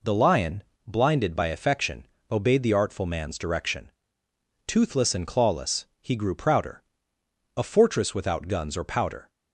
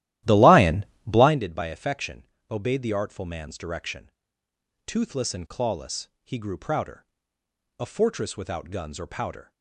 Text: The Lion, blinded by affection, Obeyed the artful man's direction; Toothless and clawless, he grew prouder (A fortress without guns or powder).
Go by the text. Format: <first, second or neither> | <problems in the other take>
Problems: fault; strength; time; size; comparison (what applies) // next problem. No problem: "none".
first | starts louder than the rest; strong; until 1.4 s; 14 dB